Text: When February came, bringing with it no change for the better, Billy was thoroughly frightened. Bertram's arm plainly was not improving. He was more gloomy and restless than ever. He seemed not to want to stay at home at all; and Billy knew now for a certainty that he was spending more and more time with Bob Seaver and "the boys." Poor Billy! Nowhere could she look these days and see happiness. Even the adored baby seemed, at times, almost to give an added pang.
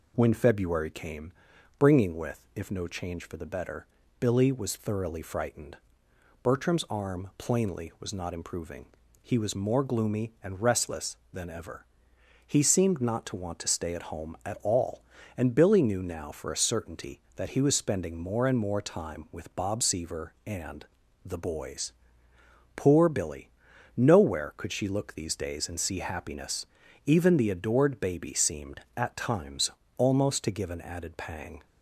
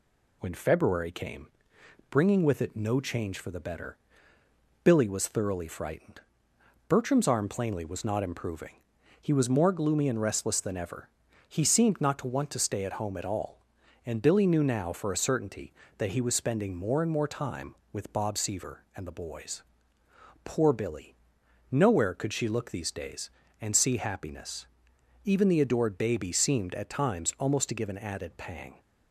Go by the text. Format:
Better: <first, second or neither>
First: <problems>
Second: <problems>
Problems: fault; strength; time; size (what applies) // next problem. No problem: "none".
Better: second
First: says "if" for "it"; at 2.5 s // pauses between "and" and "the"; at 20.8 s; 0.40 s long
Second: none